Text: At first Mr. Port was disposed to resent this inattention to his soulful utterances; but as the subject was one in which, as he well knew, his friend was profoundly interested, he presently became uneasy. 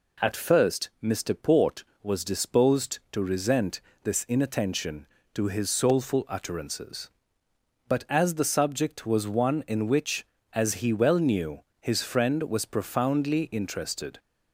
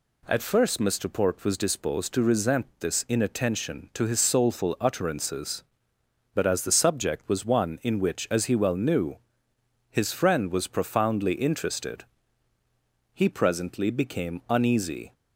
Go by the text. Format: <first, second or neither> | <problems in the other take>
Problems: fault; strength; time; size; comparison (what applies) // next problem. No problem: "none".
second | pauses between "resent" and "this"; slight; at 3.7 s; 0.22 s long // stops before "he presently became uneasy"; at 14.1 s